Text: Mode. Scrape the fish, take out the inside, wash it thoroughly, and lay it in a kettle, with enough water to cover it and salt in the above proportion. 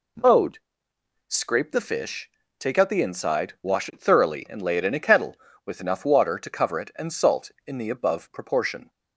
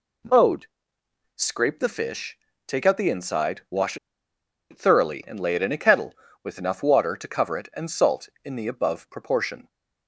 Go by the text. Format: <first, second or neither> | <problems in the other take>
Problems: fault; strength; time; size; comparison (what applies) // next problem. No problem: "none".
first | pauses between "wash" and "it"; noticeable; at 3.9 s; 0.73 s long